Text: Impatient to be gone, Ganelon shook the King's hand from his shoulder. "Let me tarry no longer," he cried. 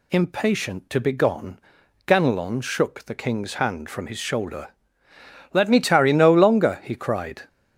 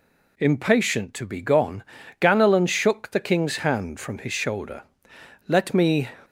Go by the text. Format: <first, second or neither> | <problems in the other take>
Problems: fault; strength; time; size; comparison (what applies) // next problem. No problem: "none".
first | stops before "tarry no longer he cried"; at 6.2 s